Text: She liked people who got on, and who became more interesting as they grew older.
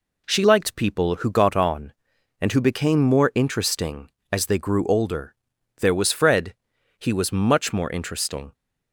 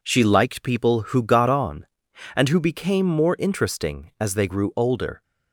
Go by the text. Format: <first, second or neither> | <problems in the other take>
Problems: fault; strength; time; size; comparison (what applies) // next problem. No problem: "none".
second | goes on to say "There was Fred he was much more interesting"; strong; from 5.8 s on; 2.7 s long